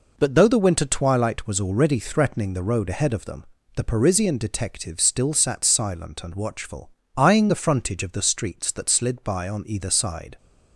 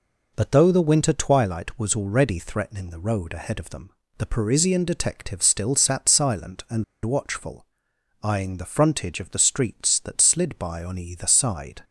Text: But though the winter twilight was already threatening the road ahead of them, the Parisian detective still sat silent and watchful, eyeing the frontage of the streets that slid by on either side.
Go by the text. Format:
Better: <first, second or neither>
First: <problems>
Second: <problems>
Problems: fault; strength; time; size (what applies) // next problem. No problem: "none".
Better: first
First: none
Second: pauses between "and" and "watchful"; slight; at 6.8 s; 0.19 s long